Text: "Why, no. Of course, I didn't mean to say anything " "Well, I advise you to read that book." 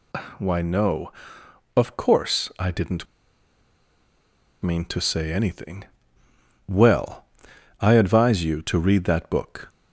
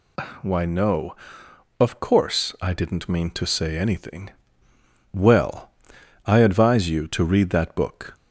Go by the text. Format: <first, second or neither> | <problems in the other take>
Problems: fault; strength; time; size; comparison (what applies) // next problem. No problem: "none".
second | pauses between "didn't" and "mean"; strong; at 3.0 s; 1.5 s long